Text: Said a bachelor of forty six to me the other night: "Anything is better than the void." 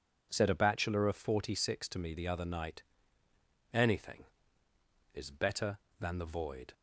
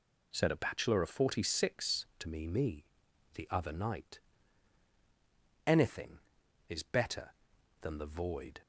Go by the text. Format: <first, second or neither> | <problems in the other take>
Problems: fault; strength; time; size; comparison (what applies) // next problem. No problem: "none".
first | says "me" twice; at 2.4 s